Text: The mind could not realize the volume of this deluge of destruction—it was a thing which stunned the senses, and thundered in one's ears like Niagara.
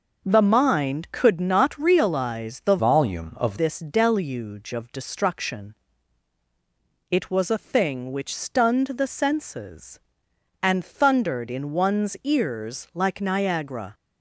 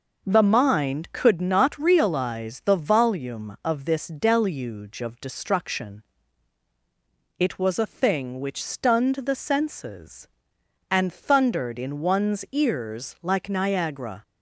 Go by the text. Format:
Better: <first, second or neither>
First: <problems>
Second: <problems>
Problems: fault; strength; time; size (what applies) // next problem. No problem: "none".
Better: second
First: changes voice from "volume" to "of"; from 2.7 to 3.5 s; 0.8 s long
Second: none